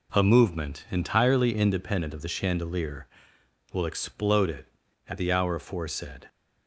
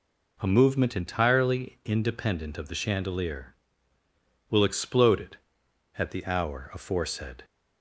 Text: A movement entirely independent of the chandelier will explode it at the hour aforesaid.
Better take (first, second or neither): neither